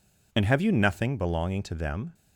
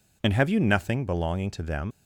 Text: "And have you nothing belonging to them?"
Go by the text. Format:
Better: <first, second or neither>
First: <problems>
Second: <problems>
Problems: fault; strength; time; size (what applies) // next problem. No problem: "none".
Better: first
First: none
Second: leaves "them" unfinished; at 1.9 s; 110 ms